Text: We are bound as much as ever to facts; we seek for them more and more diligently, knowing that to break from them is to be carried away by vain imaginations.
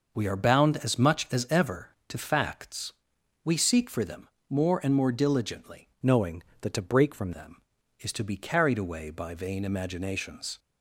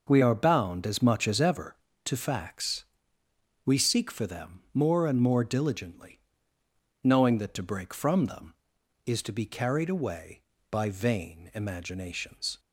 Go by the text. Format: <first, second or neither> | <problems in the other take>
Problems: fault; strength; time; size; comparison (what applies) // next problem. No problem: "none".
second | pauses between "them" and "more"; slight; at 4.2 s; 0.22 s long // changes voice from "knowing" to "from"; from 6.0 to 7.3 s; 1.3 s long